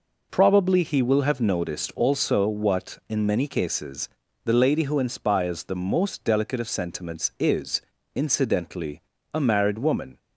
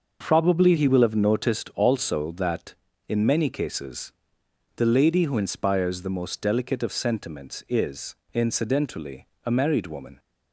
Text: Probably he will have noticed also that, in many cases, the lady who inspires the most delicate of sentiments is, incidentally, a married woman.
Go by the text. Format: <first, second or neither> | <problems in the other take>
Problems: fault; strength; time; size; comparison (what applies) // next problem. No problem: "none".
second | says "what" for "that"; at 2.4 s